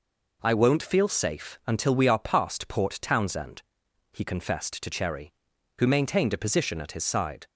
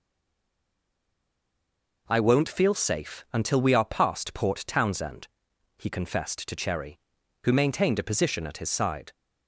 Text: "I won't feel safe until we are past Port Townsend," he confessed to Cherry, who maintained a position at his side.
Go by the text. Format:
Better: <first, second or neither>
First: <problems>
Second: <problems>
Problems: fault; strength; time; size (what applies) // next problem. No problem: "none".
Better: first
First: none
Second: stays silent before the first word; noticeable; until 2.0 s; 2.0 s long